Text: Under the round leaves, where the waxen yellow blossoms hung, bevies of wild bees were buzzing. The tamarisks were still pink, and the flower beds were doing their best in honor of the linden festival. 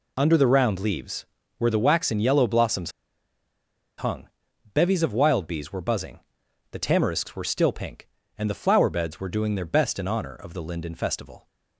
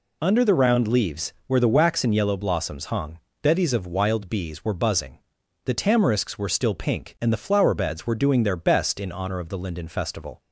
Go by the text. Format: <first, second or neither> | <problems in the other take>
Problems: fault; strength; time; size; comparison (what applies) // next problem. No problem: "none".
second | pauses between "blossoms" and "hung"; at 2.9 s; 1.0 s long